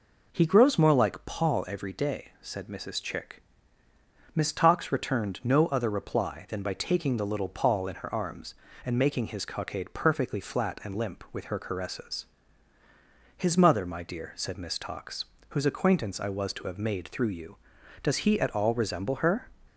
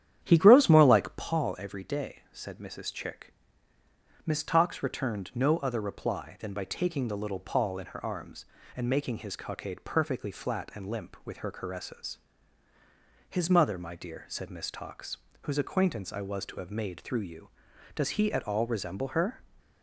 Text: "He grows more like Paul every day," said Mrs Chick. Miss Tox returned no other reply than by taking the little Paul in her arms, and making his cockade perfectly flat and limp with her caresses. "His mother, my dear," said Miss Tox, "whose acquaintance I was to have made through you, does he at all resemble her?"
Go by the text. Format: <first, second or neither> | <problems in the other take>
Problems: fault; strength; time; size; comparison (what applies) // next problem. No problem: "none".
first | starts louder than the rest; strong; until 1.4 s; 10 dB